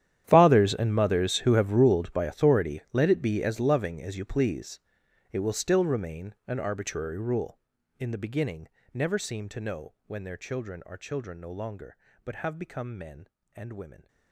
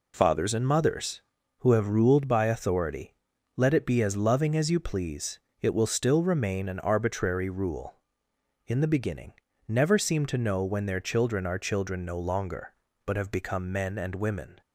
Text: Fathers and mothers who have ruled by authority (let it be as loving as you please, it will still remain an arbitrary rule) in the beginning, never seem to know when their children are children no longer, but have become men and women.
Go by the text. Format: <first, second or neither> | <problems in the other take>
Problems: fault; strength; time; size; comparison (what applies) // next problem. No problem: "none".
second | gets quieter; strong; throughout; 18.5 dB